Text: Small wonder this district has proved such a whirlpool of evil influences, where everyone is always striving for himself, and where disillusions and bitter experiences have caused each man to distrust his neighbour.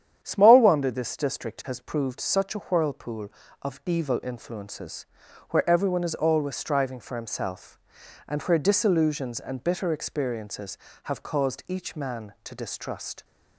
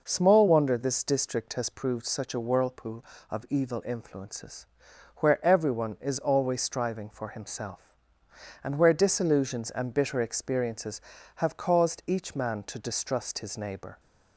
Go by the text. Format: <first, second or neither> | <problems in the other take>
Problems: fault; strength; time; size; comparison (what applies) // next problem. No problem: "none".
second | starts louder than the rest; strong; until 1.2 s; 9.5 dB // stops before "his neighbour"; at 13.2 s